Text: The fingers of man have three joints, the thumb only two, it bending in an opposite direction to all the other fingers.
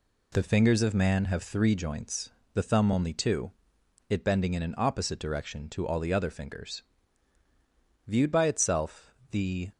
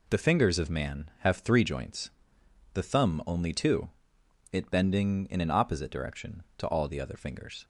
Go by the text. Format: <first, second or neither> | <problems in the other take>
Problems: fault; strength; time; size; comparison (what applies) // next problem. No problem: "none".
second | goes on to say "Viewed by itself the"; from 8.0 s on; 1.6 s long